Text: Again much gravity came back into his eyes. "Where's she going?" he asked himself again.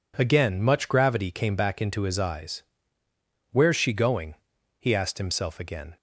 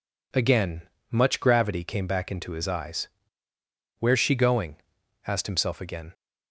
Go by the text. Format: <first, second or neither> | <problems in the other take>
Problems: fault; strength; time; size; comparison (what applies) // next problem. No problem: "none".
first | pauses between "Again" and "much"; slight; at 0.8 s; 0.30 s long // skips "he"; at 5.0 s